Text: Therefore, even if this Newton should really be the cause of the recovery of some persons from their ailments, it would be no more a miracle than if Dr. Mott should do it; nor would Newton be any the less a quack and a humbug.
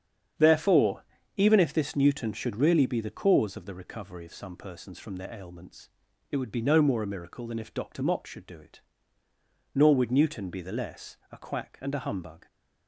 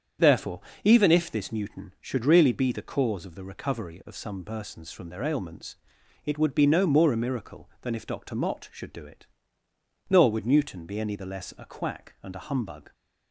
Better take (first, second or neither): second